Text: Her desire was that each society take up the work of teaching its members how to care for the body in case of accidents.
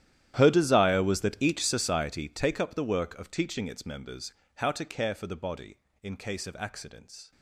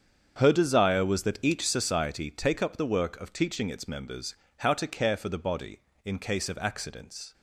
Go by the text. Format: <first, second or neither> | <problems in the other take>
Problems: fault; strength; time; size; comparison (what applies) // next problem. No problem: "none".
second | gets quieter; strong; throughout; 19.5 dB // starts louder than the rest; strong; until 1.3 s; 11.5 dB; strong in the second // pauses between "members" and "how"; slight; at 4.3 s; 0.22 s long; slight in the second